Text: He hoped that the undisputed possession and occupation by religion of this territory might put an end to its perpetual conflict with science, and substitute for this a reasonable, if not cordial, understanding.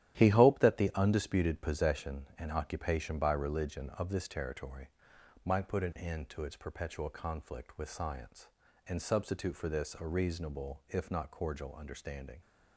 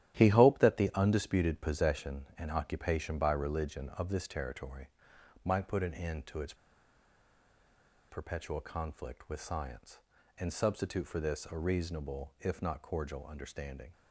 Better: first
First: starts louder than the rest; strong; until 1.2 s; 12 dB // pauses between "territory" and "might"; noticeable; at 4.8 s; 0.56 s long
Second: starts louder than the rest; strong; until 1.2 s; 12 dB // pauses between "territory" and "might"; noticeable; at 4.8 s; 0.56 s long // pauses between "its" and "perpetual"; strong; at 6.5 s; 1.5 s long

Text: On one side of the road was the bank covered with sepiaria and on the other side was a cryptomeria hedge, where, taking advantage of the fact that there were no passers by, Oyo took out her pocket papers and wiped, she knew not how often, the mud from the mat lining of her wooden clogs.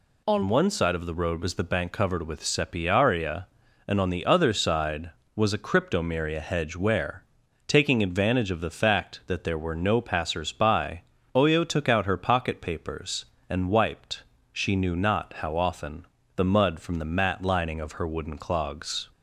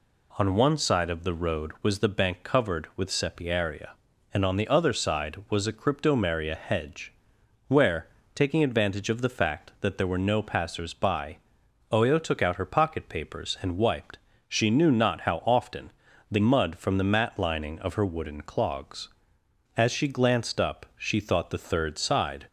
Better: first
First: none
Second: goes on to say "As she glanced up she thought the third side"; strong; from 19.7 s on; 2.7 s long

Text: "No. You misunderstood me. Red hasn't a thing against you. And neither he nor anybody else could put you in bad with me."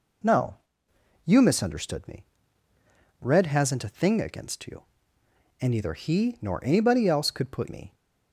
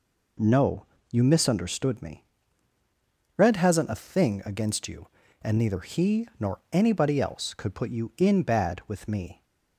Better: second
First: skips "you in bad with"; at 7.6 s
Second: none

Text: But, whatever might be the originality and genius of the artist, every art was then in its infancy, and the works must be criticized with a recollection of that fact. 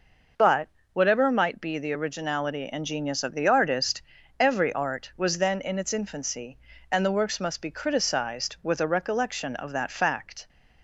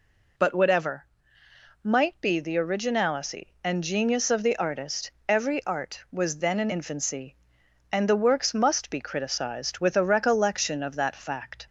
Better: first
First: none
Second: pauses between "whatever" and "might"; noticeable; at 1.0 s; 0.76 s long // skips "its"; at 6.6 s

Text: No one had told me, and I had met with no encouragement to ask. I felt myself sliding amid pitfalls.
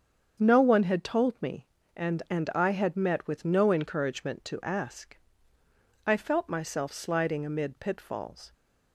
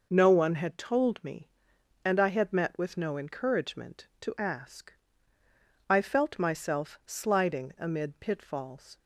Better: second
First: starts louder than the rest; strong; until 1.4 s; 7.5 dB // says "and" twice; at 2.3 s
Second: none

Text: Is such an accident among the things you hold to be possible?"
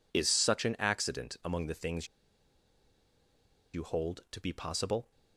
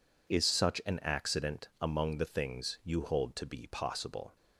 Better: second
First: pauses between "things" and "you"; strong; at 2.0 s; 1.6 s long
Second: none

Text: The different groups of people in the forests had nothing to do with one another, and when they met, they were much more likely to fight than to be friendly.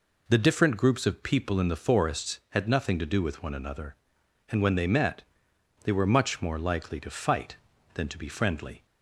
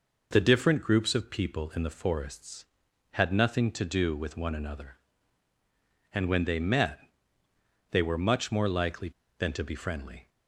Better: first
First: none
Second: skips "to fight"; at 9.2 s

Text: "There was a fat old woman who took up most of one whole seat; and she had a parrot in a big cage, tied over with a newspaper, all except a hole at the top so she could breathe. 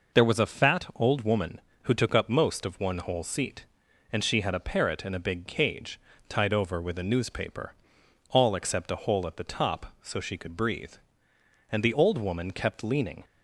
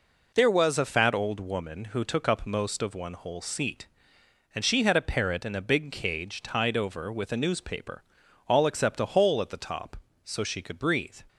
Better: second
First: goes on to say "And the old woman kept leaning"; from 11.7 s on; 1.5 s long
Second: none

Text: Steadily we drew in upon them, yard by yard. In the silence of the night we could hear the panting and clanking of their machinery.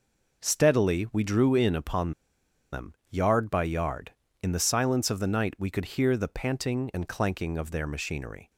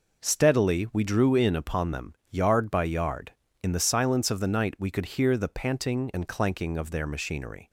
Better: second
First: pauses between "upon" and "them"; noticeable; at 2.1 s; 0.59 s long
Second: none

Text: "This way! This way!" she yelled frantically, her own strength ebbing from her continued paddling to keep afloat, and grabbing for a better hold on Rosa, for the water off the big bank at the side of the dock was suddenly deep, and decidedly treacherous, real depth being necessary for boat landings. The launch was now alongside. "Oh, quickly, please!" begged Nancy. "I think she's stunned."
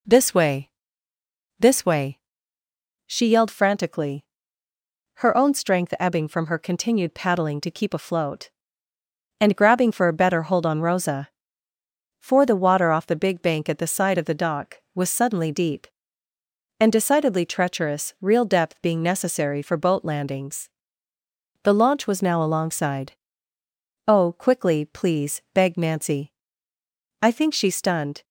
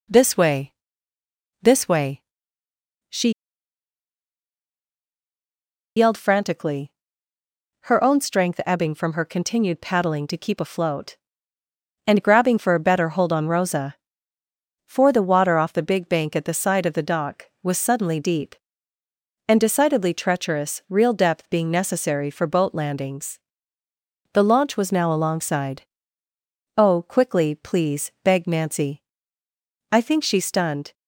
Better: first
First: none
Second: pauses between "she" and "yelled"; strong; at 3.2 s; 2.6 s long

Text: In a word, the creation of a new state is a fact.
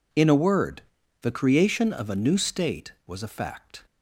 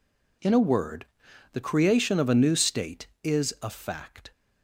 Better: second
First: says "was" for "is"; at 3.0 s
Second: none

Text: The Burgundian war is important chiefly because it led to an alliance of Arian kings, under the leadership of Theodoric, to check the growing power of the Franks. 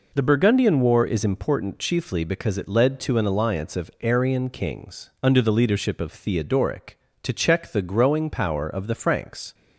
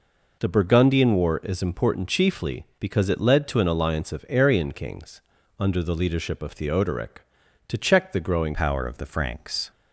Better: first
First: none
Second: changes voice at "power"; from 8.5 s on; 1.2 s long

